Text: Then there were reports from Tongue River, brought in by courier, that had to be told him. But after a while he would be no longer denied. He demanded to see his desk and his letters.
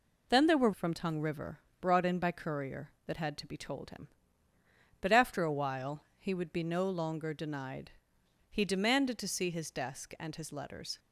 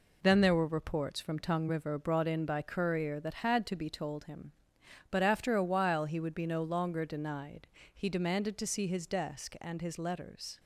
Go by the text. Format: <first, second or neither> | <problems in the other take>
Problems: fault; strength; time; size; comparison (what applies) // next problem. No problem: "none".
second | skips "reports"; at 0.7 s // pauses between "while" and "he"; slight; at 6.0 s; 0.16 s long